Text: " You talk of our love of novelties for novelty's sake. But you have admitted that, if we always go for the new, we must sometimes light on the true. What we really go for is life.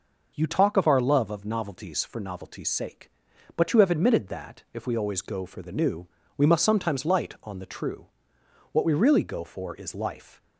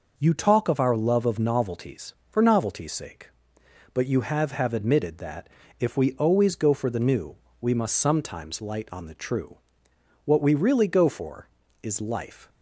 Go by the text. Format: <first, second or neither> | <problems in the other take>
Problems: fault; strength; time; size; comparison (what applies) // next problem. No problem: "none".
first | says "have" twice; at 4.5 s